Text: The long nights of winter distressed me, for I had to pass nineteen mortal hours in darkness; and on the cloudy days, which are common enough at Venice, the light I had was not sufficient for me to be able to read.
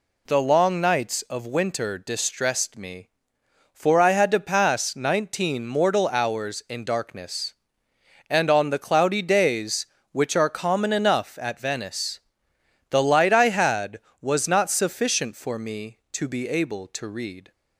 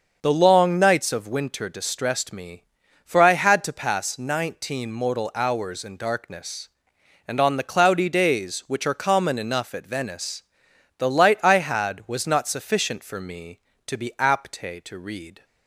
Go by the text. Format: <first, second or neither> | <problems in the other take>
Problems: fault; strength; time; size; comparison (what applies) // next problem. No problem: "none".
first | starts louder than the rest; until 1.2 s; 6 dB // says "apte" for "able"; at 14.1 s